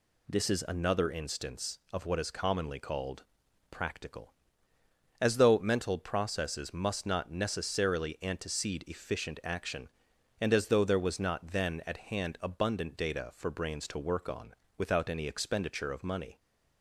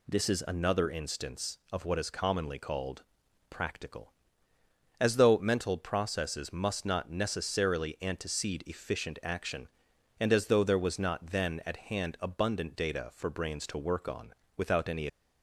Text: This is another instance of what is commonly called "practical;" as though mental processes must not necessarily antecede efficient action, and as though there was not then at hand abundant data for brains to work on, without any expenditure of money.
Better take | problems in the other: first | pauses between "called" and "practical"; noticeable; at 3.0 s; 0.46 s long; noticeable in the first // stops before "expenditure of money"; at 15.0 s

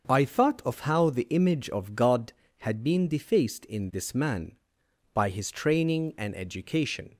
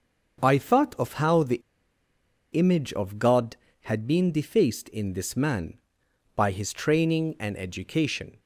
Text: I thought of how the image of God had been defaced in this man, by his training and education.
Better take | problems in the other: first | starts louder than the rest; until 1.4 s; 7 dB; also in the first // pauses between "the" and "image"; noticeable; at 1.5 s; 0.94 s long

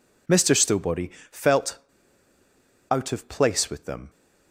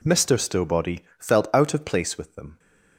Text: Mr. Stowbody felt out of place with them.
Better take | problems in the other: second | pauses between "Stowbody" and "felt"; slight; at 1.0 s; 0.20 s long; slight in the second // pauses between "felt" and "out"; at 1.7 s; 1.1 s long

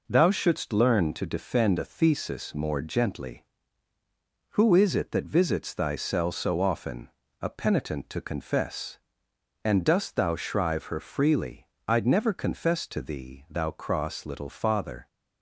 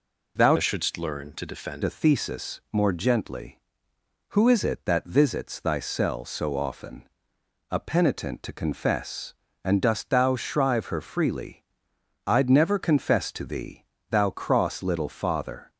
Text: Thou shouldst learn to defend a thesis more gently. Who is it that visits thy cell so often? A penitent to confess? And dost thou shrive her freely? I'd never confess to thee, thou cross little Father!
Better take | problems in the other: first | changes voice from "shouldst" to "defend"; from 0.5 to 1.8 s; 1.3 s long

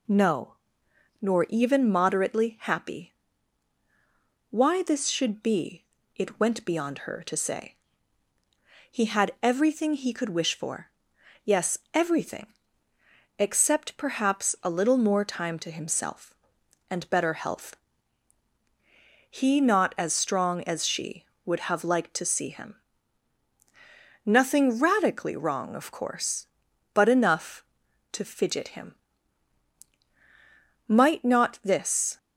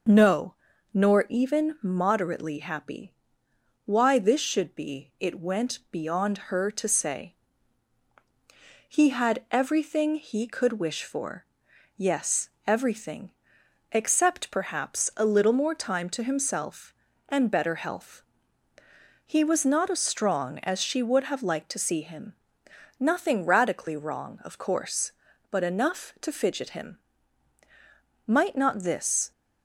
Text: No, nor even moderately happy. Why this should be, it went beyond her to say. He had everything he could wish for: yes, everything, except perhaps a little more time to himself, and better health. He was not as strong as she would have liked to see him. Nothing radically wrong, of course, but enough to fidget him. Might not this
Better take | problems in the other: second | skips "was"; at 19.5 s

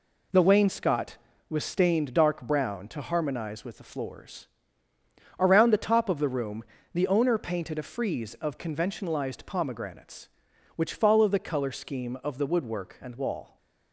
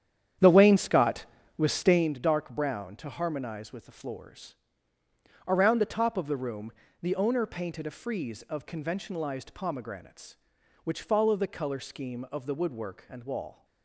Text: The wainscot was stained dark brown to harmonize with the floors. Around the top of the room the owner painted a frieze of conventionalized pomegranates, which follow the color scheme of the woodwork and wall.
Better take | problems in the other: first | starts louder than the rest; strong; until 2.2 s; 9.5 dB // pauses between "room" and "the"; slight; at 6.7 s; 0.30 s long; slight in the first

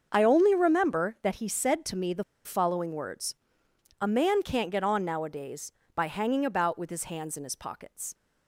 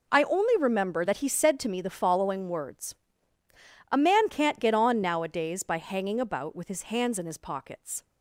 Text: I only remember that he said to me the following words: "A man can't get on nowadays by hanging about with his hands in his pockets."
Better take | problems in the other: second | starts louder than the rest; until 1.1 s; 6.5 dB // pauses between "the" and "following"; slight; at 2.2 s; 0.22 s long

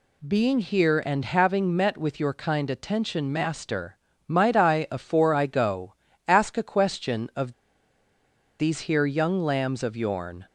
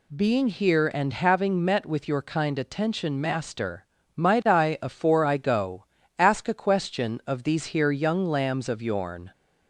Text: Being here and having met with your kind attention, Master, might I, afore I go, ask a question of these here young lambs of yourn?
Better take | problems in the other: second | pauses between "of" and "these"; at 7.5 s; 1.0 s long

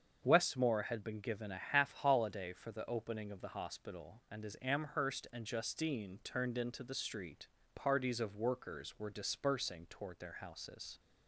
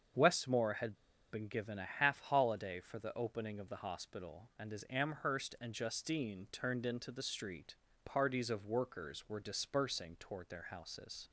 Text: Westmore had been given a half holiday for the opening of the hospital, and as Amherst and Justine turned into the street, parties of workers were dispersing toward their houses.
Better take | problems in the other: first | starts louder than the rest; strong; until 1.5 s; 7 dB; strong in the first // pauses between "had" and "been"; at 0.9 s; 0.37 s long

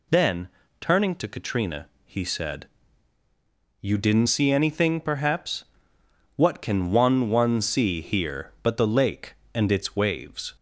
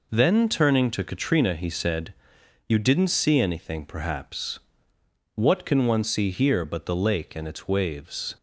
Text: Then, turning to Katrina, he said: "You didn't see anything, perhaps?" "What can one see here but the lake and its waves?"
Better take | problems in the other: second | says "one" twice; at 7.2 s

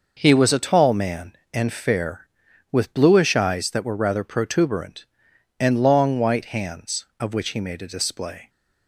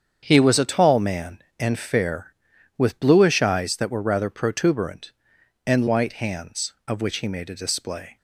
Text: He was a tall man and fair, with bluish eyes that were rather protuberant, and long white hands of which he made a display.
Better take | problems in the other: first | starts louder than the rest; strong; until 1.2 s; 7.5 dB // skips "long"; at 5.8 s

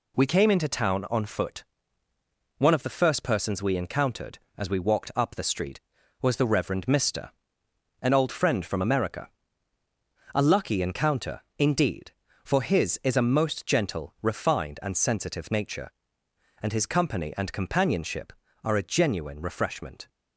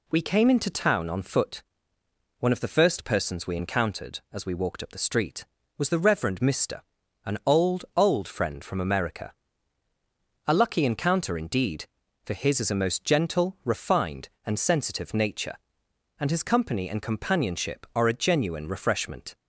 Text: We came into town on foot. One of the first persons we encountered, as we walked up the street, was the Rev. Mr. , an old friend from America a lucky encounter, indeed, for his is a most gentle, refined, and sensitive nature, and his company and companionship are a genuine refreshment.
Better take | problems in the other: first | says "old" twice; at 7.9 s // pauses between "America" and "a"; at 9.3 s; 1.1 s long; also in the first

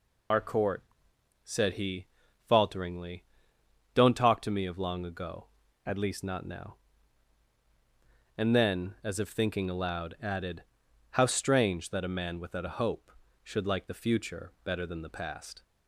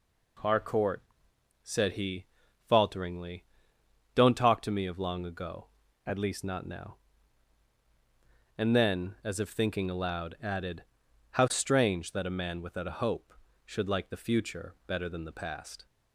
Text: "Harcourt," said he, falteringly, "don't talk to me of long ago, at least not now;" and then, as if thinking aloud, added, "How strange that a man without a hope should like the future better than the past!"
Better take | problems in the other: second | loses the start of "Harcourt"; at 0.3 s; 125 ms

